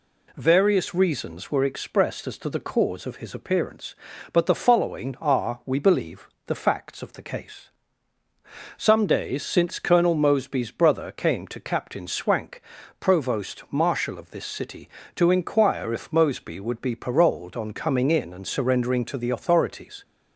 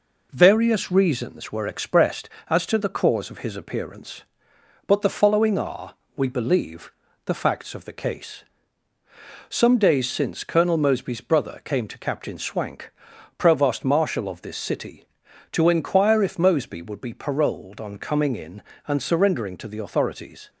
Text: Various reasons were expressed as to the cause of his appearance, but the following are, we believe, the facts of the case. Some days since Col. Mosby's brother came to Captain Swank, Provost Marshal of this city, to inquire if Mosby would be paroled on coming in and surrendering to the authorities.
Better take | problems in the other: first | gets quieter; slight; throughout; 2 dB

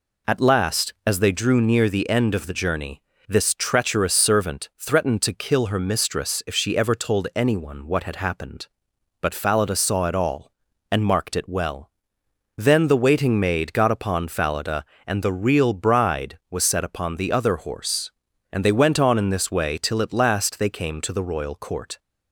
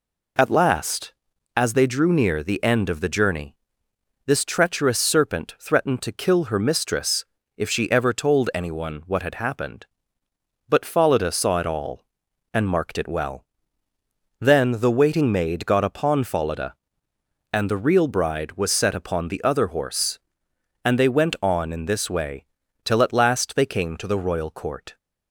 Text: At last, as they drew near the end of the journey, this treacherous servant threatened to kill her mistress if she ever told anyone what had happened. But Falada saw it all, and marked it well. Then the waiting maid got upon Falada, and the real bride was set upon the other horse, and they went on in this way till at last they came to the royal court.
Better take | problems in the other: first | says "serpent" for "servant"; at 4.9 s // pauses between "mistress" and "if"; slight; at 7.2 s; 0.32 s long // pauses between "way" and "till"; at 22.4 s; 0.40 s long

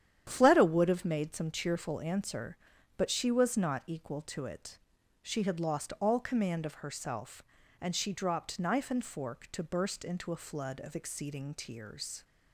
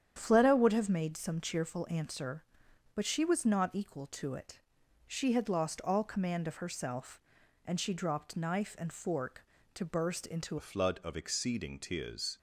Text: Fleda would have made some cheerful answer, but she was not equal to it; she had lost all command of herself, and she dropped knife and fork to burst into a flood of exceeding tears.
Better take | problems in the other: first | starts louder than the rest; strong; until 1.1 s; 9 dB; strong in the first // changes voice at "a"; from 10.5 s on; 1.8 s long

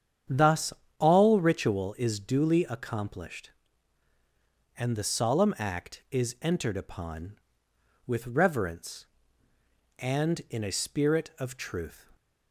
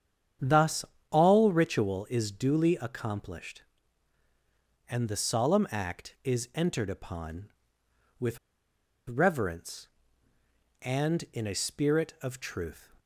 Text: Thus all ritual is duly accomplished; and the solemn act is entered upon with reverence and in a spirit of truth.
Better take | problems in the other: first | starts louder than the rest; strong; until 1.6 s; 8.5 dB; strong in the first // pauses between "Thus" and "all"; slight; at 0.8 s; 0.24 s long; slight in the first // pauses between "with" and "reverence"; noticeable; at 8.3 s; 0.71 s long

